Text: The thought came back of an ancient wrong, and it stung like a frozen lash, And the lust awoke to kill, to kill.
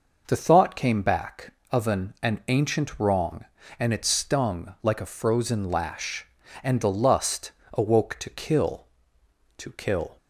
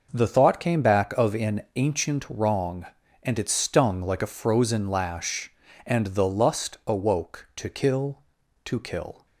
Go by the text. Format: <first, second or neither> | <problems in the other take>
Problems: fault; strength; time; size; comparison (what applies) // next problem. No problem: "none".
second | says "an" twice; at 2.2 s // pauses between "lust" and "awoke"; slight; at 7.5 s; 0.24 s long